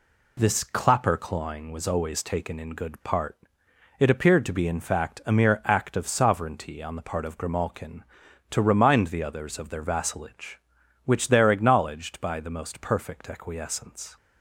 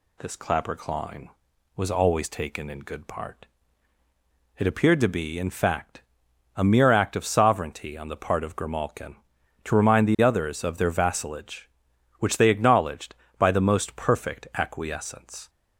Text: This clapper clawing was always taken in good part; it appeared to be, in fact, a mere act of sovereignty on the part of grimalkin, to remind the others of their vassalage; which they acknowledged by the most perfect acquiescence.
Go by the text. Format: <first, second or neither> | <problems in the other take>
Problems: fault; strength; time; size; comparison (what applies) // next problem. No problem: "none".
second | says "there" for "they"; at 11.2 s